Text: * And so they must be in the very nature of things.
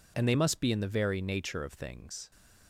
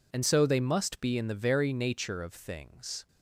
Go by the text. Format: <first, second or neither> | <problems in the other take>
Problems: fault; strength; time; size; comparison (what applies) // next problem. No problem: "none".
second | skips "so"; at 0.2 s